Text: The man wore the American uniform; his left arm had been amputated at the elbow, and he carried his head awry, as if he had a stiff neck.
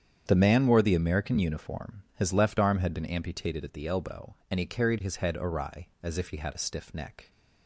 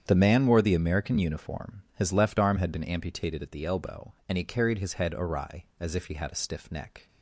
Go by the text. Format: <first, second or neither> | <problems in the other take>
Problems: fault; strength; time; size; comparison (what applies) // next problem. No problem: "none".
neither | starts louder than the rest; strong; the same in both